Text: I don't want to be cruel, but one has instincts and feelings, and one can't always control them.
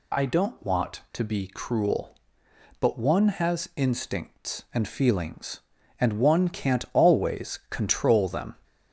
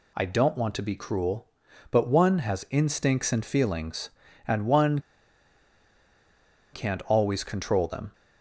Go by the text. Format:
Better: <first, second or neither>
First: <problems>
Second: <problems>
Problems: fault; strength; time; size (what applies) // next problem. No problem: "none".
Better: first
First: none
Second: pauses between "one" and "can't"; strong; at 4.9 s; 1.7 s long